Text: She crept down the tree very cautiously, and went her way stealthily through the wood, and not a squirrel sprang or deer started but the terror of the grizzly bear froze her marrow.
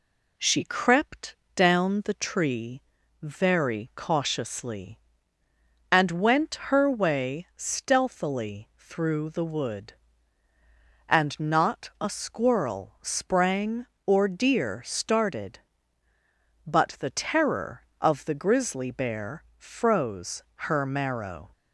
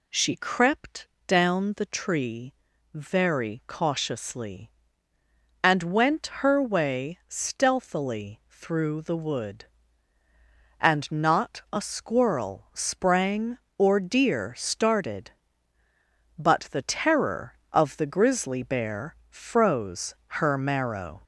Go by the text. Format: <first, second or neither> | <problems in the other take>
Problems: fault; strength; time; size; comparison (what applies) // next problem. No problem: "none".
first | gets louder; slight; throughout; 3 dB // pauses between "crept" and "down"; slight; at 1.0 s; 0.18 s long; slight in the first // pauses between "tree" and "very"; at 2.5 s; 0.40 s long; also in the first